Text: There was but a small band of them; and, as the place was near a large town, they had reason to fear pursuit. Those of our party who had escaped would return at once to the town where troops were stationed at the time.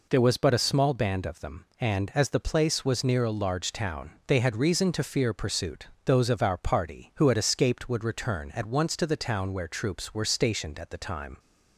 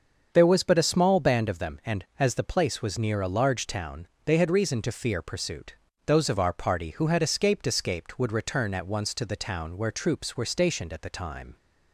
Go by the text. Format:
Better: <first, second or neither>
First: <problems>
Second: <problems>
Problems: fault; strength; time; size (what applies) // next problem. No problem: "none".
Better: first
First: none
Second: starts louder than the rest; until 1.3 s; 7 dB // says "escaped" twice; at 7.6 s